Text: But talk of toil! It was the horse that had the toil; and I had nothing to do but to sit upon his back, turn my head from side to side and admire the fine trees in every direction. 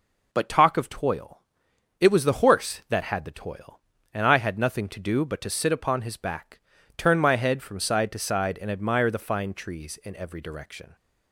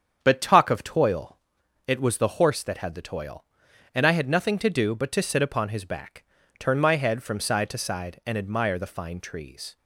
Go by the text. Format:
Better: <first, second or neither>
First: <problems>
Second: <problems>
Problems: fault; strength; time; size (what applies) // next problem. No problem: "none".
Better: first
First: none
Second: starts louder than the rest; strong; until 1.2 s; 7.5 dB // stops before "in every direction"; at 9.7 s